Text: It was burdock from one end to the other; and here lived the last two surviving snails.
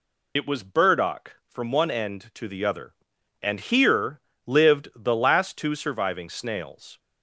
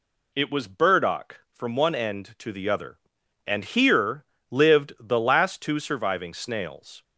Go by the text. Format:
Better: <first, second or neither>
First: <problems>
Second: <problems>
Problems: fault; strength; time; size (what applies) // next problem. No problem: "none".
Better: second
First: loses the start of "It"; at 0.3 s; 50 ms // pauses between "here" and "lived"; slight; at 4.2 s; 0.26 s long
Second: pauses between "here" and "lived"; slight; at 4.2 s; 0.26 s long